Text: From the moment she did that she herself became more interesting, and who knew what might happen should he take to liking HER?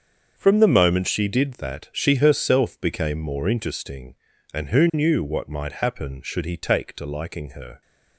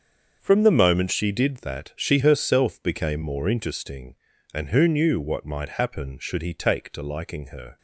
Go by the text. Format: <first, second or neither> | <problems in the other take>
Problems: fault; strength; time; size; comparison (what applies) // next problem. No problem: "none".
neither | starts louder than the rest; the same in both